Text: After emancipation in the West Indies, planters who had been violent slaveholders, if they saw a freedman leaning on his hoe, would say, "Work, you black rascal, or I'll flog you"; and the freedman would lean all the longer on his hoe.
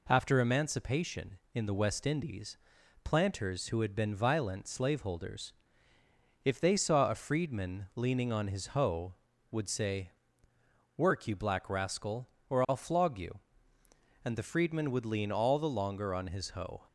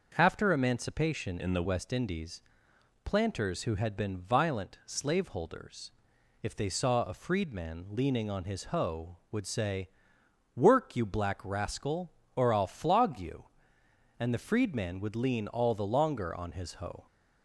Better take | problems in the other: first | starts louder than the rest; noticeable; until 1.1 s; 6 dB // changes voice from "in" to "the"; from 1.3 to 1.6 s; 0.3 s long

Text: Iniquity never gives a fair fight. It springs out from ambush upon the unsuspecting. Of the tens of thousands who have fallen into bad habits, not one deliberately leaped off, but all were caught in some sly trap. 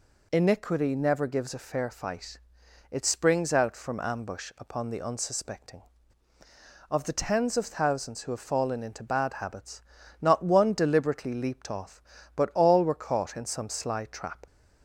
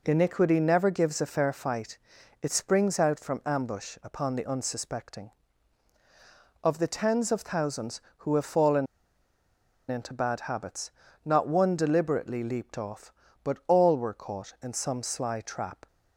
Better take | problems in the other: first | pauses between "fallen" and "into"; at 8.8 s; 1.0 s long

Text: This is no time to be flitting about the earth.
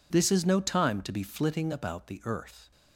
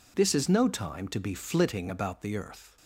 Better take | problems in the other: neither | none

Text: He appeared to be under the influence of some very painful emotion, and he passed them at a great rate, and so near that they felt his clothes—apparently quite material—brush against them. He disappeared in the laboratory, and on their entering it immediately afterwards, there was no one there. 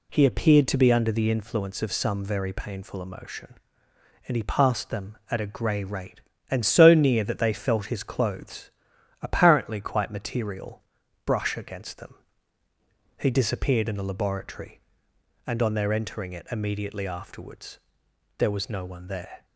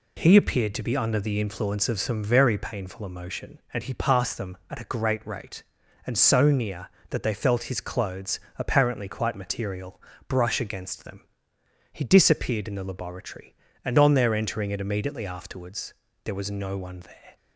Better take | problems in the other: second | says "grey" for "great"; at 5.4 s

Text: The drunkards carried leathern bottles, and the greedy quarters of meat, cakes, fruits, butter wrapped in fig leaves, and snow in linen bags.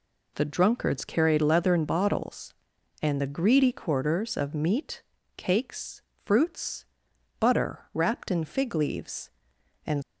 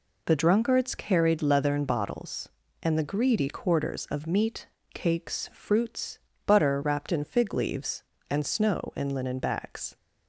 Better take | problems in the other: second | stops before "snow in linen bags"; at 10.0 s

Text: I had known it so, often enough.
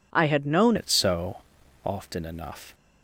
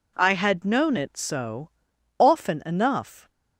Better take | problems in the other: second | changes voice at "it"; from 0.7 s on; 2.0 s long

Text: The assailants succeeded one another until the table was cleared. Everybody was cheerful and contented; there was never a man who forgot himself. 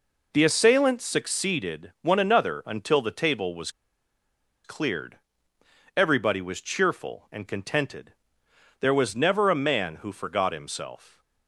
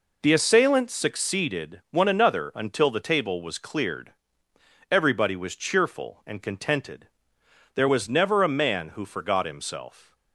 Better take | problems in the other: second | pauses between "was" and "cleared"; noticeable; at 3.6 s; 0.94 s long

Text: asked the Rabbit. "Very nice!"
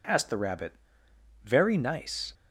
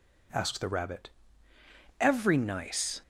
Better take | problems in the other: first | says "Every" for "Very"; at 1.9 s

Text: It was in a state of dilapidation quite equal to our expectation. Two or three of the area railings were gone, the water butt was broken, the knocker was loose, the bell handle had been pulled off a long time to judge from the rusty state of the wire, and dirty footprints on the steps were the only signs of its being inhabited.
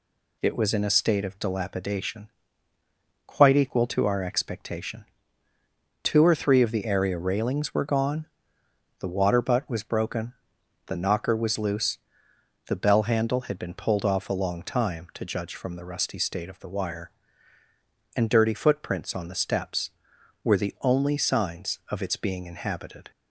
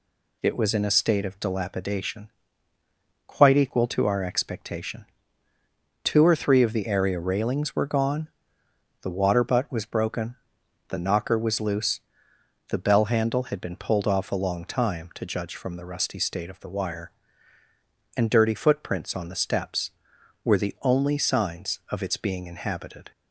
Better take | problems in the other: neither | pauses between "dilapidation" and "quite"; noticeable; the same in both

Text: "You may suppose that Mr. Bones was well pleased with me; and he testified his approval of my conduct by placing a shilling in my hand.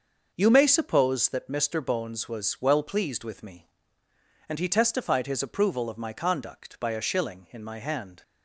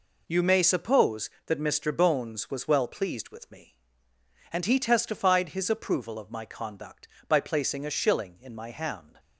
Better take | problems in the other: second | starts louder than the rest; until 1.3 s; 6.5 dB // skips "placing"; at 6.9 s

